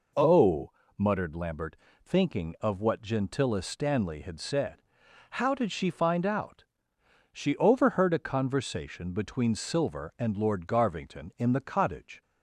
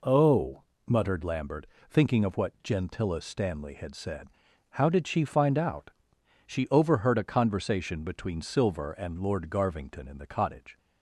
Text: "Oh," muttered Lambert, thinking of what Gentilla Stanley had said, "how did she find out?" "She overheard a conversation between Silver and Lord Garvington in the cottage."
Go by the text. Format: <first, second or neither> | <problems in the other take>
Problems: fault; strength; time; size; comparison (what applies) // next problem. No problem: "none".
neither | none